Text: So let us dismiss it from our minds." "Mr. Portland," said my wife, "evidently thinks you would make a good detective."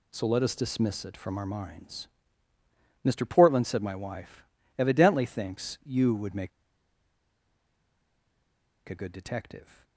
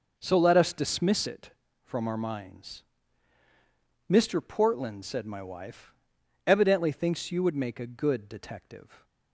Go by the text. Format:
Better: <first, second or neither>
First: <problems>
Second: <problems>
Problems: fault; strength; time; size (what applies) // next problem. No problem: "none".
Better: second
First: pauses between "make" and "a"; strong; at 6.5 s; 2.3 s long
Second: none